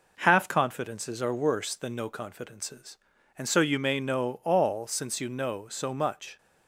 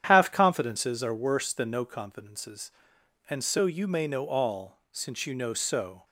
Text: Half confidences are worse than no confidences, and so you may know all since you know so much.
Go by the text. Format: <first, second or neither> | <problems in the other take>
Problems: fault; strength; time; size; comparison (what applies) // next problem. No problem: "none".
first | starts louder than the rest; strong; until 1.0 s; 9.5 dB // stops before "much"; at 6.0 s